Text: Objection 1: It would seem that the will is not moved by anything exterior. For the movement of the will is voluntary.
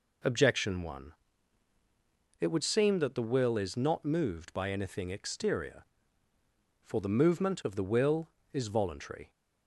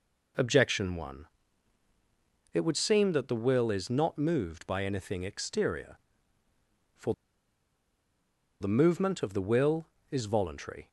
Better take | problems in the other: first | pauses between "For" and "the"; strong; at 7.1 s; 1.4 s long

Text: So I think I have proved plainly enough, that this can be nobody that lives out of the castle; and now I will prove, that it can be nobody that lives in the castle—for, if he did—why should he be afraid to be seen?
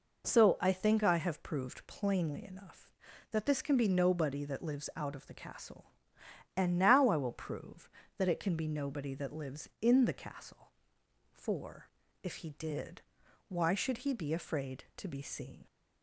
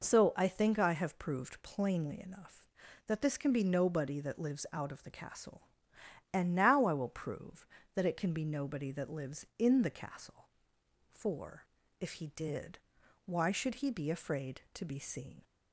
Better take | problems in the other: neither | none

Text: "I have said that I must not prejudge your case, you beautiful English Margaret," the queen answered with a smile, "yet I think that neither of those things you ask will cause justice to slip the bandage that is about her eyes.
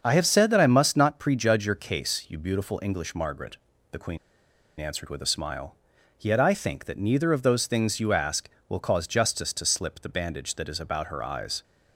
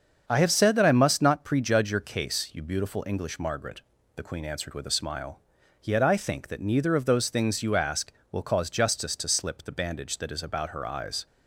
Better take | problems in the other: second | starts louder than the rest; until 1.0 s; 7 dB; also in the second // pauses between "queen" and "answered"; noticeable; at 4.1 s; 0.60 s long

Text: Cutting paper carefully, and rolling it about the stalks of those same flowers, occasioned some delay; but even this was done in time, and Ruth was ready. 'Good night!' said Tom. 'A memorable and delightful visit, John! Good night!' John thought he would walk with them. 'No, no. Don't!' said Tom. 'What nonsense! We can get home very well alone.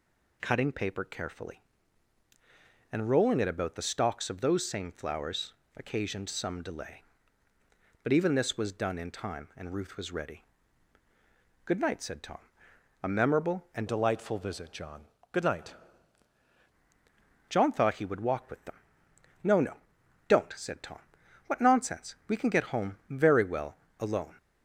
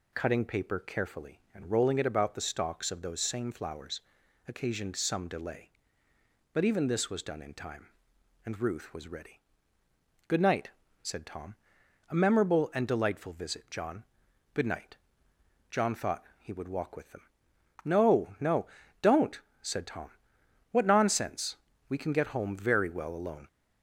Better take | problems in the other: second | changes voice from "delightful" to "night"; from 13.8 to 15.7 s; 1.9 s long // pauses between "well" and "alone"; slight; at 23.7 s; 0.22 s long

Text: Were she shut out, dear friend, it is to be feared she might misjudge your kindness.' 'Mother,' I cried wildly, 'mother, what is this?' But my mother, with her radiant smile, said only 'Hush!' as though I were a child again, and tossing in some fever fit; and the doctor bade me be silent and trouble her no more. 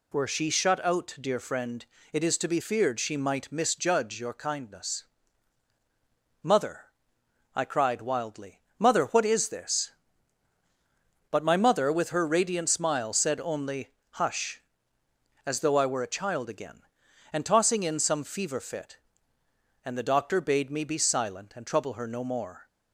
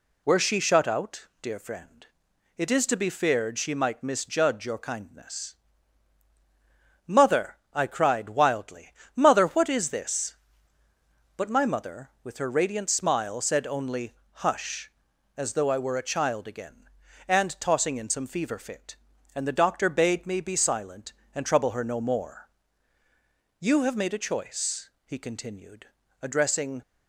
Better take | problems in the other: first | pauses between "only" and "Hush"; slight; at 14.1 s; 0.20 s long; slight in the first // goes on to say "You have made a choice he continued addressing"; strong; from 23.6 s on; 3.2 s long

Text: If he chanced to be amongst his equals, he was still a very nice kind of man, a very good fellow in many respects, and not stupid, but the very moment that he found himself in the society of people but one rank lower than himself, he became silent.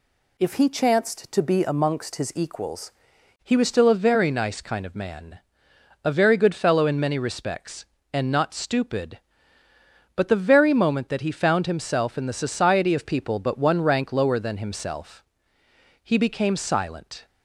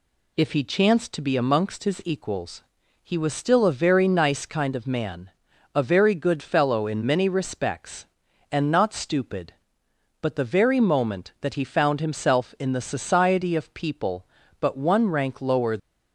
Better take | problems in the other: first | stops before "than himself he became silent"; at 15.7 s

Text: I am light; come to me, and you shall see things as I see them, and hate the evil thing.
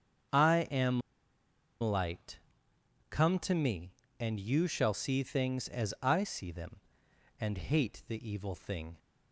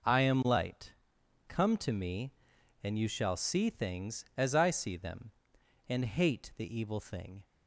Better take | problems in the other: second | starts louder than the rest; strong; until 2.1 s; 7.5 dB // pauses between "am" and "light"; noticeable; at 1.0 s; 0.80 s long

